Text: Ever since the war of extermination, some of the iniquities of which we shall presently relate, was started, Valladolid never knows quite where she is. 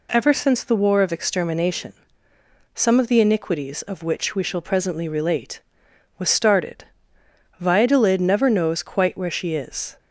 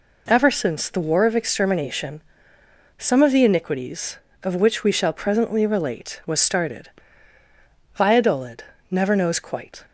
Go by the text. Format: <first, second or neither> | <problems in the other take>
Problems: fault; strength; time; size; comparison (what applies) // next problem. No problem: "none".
first | pauses between "Valladolid" and "never"; slight; at 8.6 s; 0.26 s long // stops before "where she is"; at 9.8 s